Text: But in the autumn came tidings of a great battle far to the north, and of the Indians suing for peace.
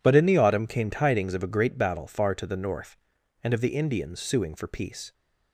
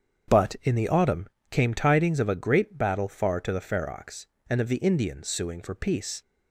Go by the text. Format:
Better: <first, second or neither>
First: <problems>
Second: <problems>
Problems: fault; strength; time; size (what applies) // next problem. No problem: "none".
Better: first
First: none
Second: starts louder than the rest; strong; until 1.5 s; 7.5 dB // pauses between "autumn" and "came"; slight; at 1.2 s; 0.22 s long // says "ferox" for "north"; at 3.6 s